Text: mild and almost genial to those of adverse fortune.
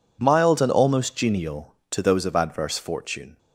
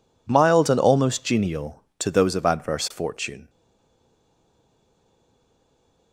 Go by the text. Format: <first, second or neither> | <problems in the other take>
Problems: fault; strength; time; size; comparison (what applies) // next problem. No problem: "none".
first | stays silent after the last word; strong; from 3.4 s on; 2.7 s long